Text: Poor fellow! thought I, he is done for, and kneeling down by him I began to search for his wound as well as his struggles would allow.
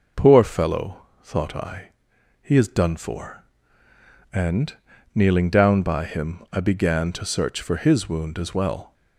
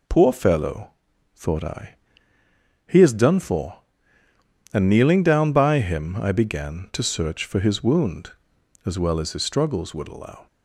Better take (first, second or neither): second